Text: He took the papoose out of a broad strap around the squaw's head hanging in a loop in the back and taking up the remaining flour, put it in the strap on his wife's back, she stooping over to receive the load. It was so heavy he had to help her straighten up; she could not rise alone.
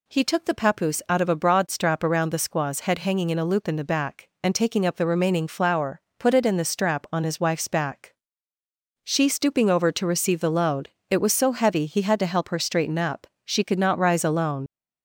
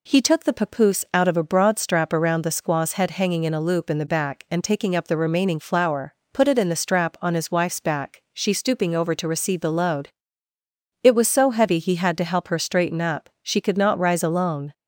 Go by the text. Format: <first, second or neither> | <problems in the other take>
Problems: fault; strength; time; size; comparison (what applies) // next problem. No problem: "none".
second | leaves "alone" unfinished; at 14.6 s; 50 ms